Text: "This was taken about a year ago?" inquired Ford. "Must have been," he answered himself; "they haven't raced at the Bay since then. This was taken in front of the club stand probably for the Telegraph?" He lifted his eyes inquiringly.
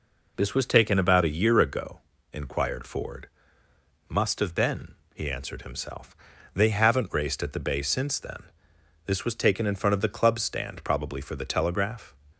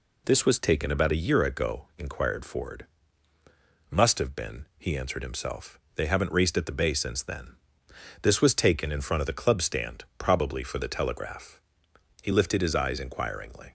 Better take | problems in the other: second | stops before "He lifted his eyes inquiringly"; at 12.3 s

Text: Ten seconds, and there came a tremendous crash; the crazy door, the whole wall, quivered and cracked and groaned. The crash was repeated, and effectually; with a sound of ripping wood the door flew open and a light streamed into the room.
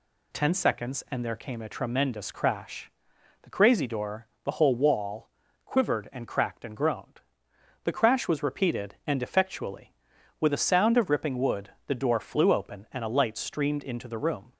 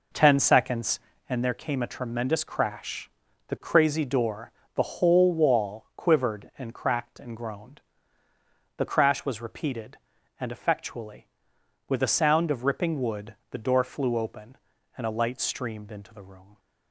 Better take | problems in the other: first | starts louder than the rest; noticeable; until 1.5 s; 5 dB // pauses between "wood" and "the"; slight; at 13.3 s; 0.16 s long; slight in the first

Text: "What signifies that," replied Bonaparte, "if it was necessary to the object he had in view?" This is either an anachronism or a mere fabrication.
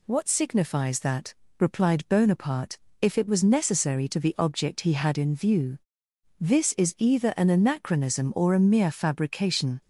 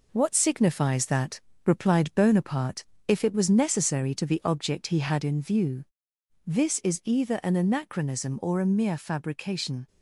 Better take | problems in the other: first | gets quieter; noticeable; throughout; 4 dB

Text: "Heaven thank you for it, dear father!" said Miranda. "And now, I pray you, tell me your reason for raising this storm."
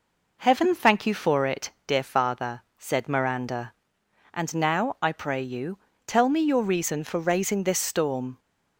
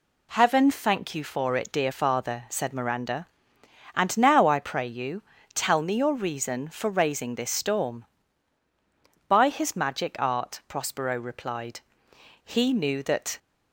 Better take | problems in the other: first | goes on to say "By his magic art Prospero replied he knew that"; strong; from 9.2 s on; 4.1 s long

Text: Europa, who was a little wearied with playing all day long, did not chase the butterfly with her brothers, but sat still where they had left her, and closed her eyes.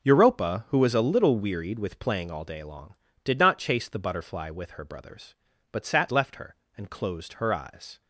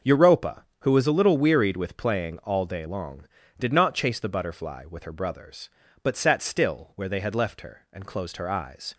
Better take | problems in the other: second | skips "still where they had"; at 6.0 s

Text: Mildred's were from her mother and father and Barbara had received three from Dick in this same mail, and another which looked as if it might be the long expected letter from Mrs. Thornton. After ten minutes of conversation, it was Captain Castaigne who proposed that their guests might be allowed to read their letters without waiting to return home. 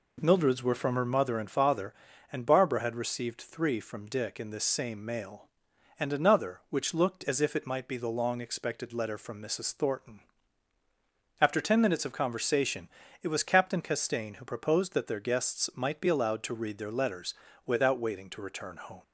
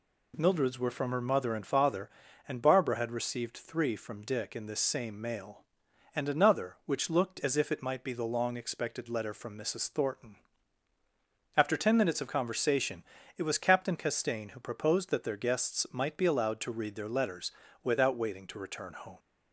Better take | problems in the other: second | starts louder than the rest; until 1.3 s; 3.5 dB // pauses between "letters" and "without"; slight; at 17.3 s; 0.32 s long; slight in the second

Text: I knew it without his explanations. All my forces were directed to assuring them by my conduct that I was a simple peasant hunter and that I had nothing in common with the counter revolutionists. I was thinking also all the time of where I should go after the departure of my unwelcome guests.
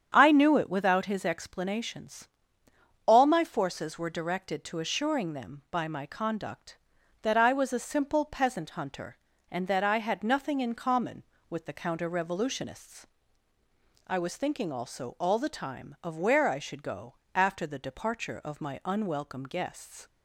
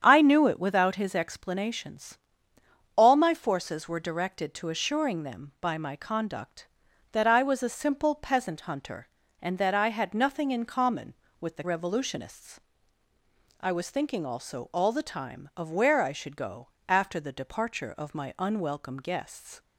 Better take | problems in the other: first | starts louder than the rest; strong; until 1.0 s; 8.5 dB; strong in the first // skips "counter"; at 11.6 s // pauses between "go" and "after"; slight; at 16.6 s; 0.20 s long; slight in the first

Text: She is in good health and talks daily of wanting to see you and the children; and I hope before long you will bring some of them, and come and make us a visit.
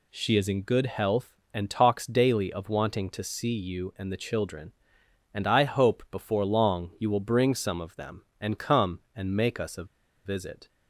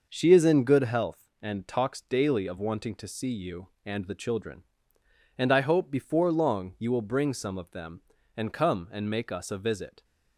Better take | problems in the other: second | pauses between "a" and "visit"; at 9.8 s; 0.40 s long

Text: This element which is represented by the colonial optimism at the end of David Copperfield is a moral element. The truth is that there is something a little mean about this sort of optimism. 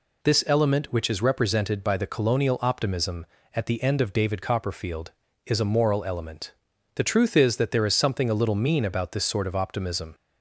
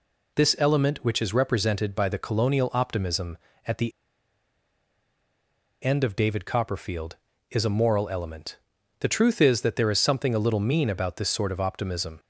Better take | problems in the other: first | pauses between "the" and "end"; strong; at 3.9 s; 1.9 s long

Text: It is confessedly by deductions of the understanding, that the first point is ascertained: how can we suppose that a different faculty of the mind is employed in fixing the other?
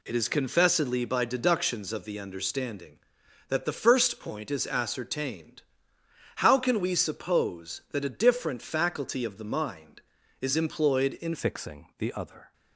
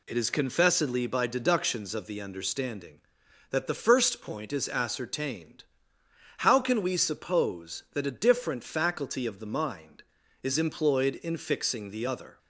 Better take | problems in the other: second | changes voice at "fixing"; from 11.3 s on; 1.2 s long

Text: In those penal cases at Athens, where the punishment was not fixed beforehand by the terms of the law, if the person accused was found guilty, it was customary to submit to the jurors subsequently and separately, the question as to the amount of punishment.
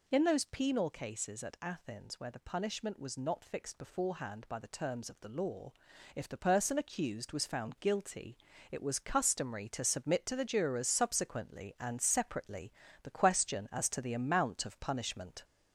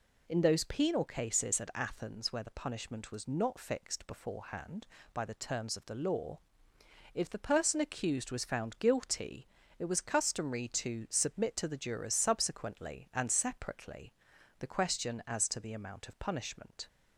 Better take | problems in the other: second | gets louder; noticeable; throughout; 4 dB

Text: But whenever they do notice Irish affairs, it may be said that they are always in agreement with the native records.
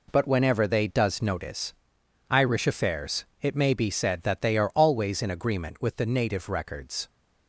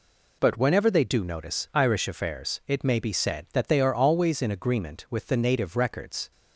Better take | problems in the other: second | says "does" for "do"; at 0.8 s // pauses between "notice" and "Irish"; noticeable; at 1.7 s; 0.58 s long

